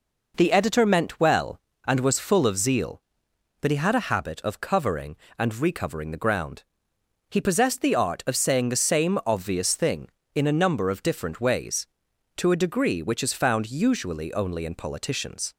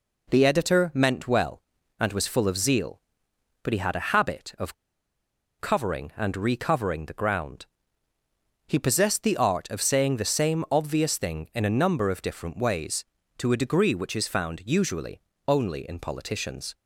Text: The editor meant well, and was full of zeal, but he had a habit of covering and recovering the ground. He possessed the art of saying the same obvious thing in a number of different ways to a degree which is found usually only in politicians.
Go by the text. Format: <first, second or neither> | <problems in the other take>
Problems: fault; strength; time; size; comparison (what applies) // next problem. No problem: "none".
first | pauses between "of" and "covering"; noticeable; at 4.7 s; 0.85 s long // pauses between "usually" and "only"; slight; at 15.2 s; 0.26 s long